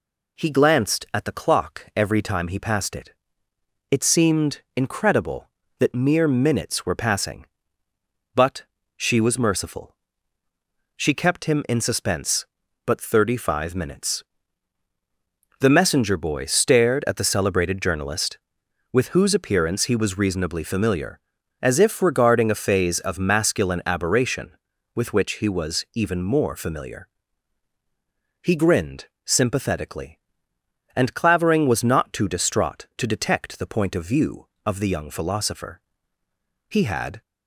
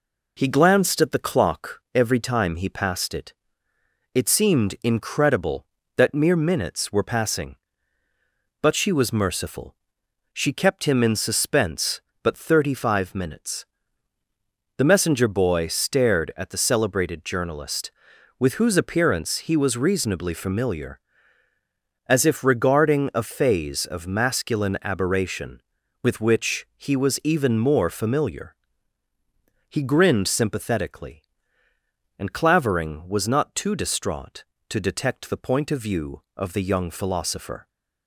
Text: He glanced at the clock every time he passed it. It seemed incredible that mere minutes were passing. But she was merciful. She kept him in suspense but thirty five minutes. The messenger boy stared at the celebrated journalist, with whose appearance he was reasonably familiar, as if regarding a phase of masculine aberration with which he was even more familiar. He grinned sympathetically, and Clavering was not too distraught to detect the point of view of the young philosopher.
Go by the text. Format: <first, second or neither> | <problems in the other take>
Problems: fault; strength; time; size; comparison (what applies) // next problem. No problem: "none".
second | pauses between "But" and "she"; slight; at 8.6 s; 0.32 s long // pauses between "grinned" and "sympathetically"; slight; at 29.0 s; 0.18 s long // goes on to say "He had"; from 36.6 s on; 0.52 s long